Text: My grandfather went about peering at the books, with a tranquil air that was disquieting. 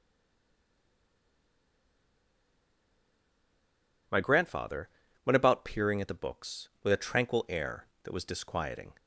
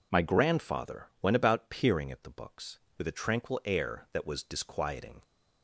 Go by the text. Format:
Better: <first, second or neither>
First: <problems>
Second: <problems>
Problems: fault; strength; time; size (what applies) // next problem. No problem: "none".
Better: second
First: stays silent before the first word; strong; until 4.1 s; 4.1 s long // pauses between "grandfather" and "went"; at 4.8 s; 0.38 s long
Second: pauses between "grandfather" and "went"; slight; at 1.0 s; 0.16 s long